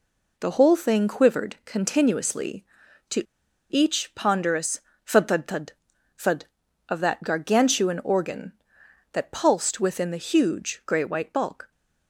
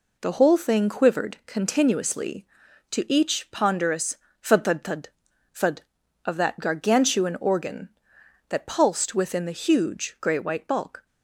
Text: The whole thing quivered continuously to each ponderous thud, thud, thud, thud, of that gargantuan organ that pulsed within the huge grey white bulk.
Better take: second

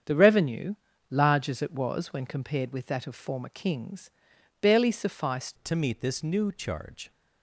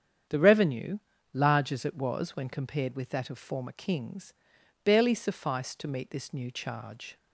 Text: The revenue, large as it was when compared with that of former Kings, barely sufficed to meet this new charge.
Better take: second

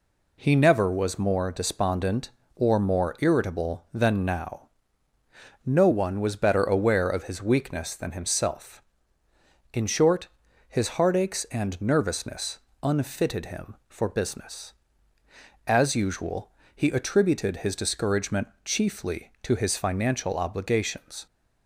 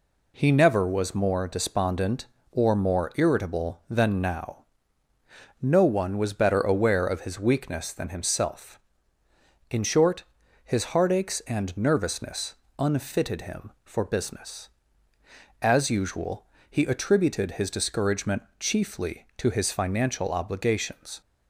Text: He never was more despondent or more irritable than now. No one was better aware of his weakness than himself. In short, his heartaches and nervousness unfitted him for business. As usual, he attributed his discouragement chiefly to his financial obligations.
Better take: neither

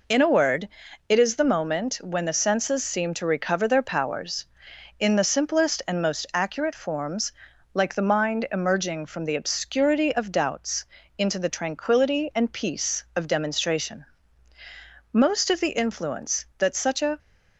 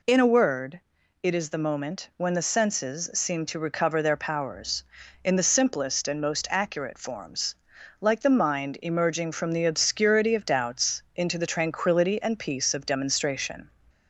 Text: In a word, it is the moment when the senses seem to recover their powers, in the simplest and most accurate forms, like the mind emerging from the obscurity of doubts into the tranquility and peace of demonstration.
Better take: second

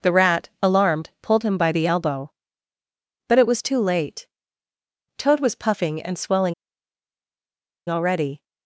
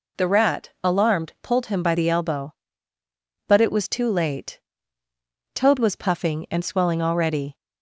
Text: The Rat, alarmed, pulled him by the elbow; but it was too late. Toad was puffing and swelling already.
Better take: second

